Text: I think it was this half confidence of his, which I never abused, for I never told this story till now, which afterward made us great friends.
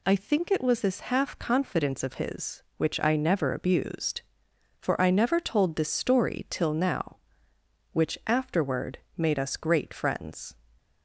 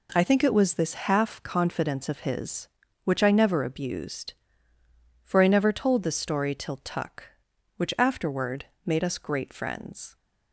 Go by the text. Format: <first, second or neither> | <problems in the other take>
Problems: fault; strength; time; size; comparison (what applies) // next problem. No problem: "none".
first | says "tuck" for "now"; at 6.8 s // pauses between "afterward" and "made"; slight; at 8.6 s; 0.20 s long; slight in the first